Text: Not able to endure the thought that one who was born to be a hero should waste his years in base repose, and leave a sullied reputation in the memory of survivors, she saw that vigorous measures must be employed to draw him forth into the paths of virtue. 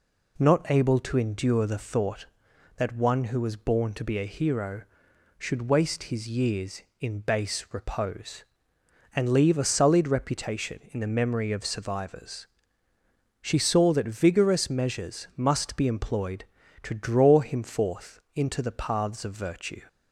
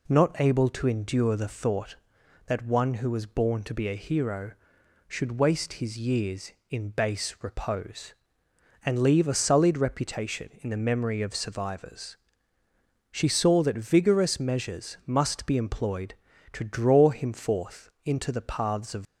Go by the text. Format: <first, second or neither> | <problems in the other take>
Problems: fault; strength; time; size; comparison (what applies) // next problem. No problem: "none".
first | pauses between "forth" and "into"; slight; at 17.8 s; 0.16 s long; slight in the first // stops before "virtue"; at 19.0 s